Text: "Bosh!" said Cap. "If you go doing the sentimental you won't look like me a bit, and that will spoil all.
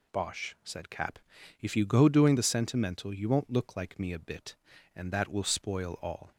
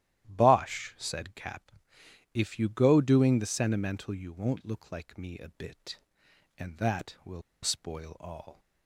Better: first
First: none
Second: starts louder than the rest; strong; until 1.2 s; 13 dB // pauses between "will" and "spoil"; slight; at 7.4 s; 0.21 s long

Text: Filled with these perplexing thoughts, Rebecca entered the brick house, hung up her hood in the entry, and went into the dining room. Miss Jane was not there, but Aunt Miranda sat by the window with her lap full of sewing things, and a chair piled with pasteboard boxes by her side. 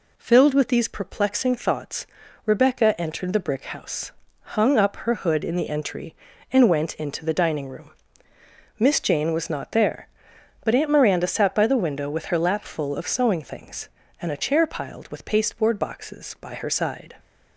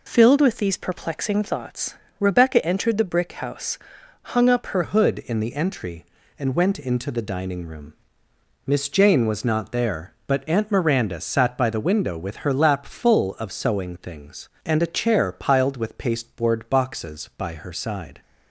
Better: first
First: none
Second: changes voice at "hood"; from 4.8 s on; 13.4 s long

